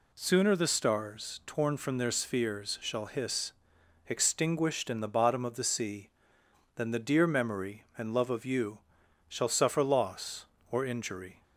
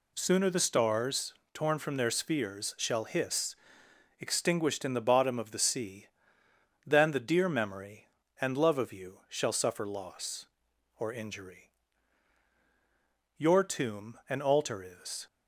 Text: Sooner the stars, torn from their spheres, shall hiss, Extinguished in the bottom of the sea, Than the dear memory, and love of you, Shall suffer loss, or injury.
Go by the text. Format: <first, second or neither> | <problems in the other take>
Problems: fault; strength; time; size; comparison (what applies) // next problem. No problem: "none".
first | goes on to say "Your tomb an altar is"; strong; from 13.3 s on; 1.9 s long